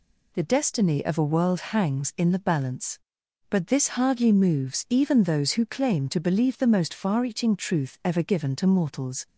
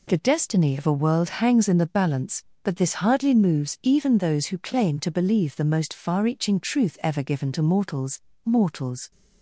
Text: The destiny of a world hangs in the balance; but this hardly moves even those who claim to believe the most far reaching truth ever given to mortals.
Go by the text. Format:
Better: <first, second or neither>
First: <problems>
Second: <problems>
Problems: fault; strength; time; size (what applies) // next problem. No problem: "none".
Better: first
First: none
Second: says "mortals" twice; at 8.4 s